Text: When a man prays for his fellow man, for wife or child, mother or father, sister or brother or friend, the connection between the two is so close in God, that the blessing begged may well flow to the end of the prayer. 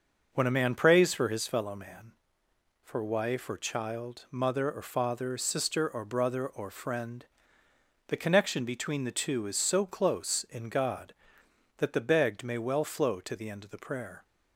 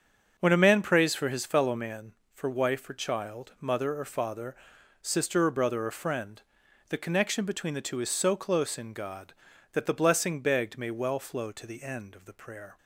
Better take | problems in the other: second | starts louder than the rest; noticeable; until 1.3 s; 6 dB; also in the second // skips "blessing"; at 11.9 s

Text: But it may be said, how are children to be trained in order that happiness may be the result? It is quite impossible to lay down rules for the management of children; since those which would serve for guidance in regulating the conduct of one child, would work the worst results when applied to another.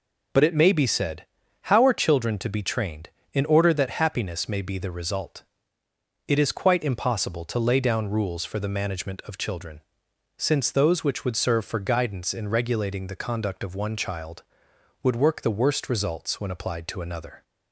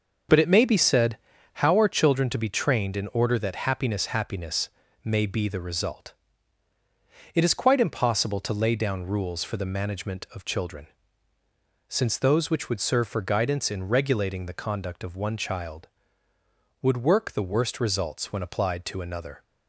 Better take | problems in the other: first | starts louder than the rest; noticeable; until 1.6 s; 6 dB // says "happiness" twice; at 4.0 s

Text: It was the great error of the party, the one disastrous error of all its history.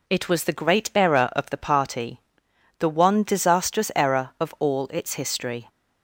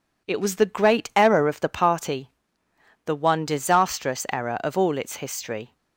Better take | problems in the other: neither | none

